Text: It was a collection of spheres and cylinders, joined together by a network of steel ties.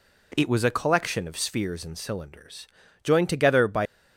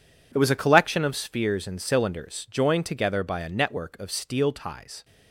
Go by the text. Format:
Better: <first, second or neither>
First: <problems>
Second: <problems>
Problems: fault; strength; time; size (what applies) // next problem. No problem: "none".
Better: second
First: stops before "a network of steel ties"; at 3.8 s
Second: none